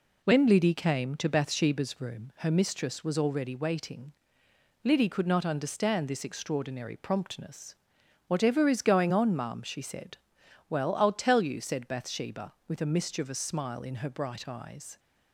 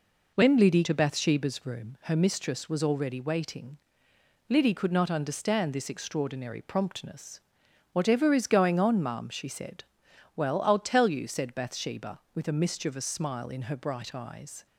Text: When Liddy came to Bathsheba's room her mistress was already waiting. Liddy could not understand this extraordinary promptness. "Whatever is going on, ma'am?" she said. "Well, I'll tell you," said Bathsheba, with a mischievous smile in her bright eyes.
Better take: first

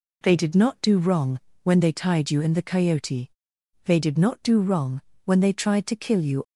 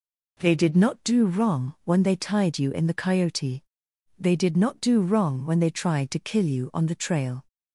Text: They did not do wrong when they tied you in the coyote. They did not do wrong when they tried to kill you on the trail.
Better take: second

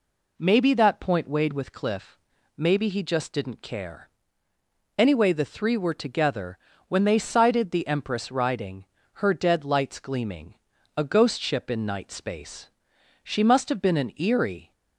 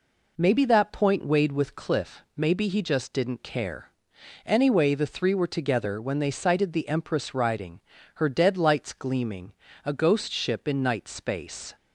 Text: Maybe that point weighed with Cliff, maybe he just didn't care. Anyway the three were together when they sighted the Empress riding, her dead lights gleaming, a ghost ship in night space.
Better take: second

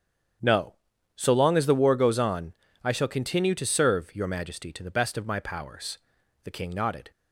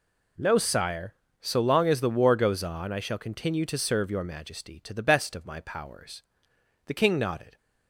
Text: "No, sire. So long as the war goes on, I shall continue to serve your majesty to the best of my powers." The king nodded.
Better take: second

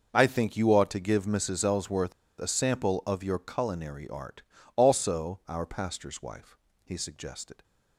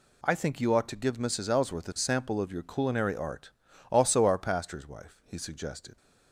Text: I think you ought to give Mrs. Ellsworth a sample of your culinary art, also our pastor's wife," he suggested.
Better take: second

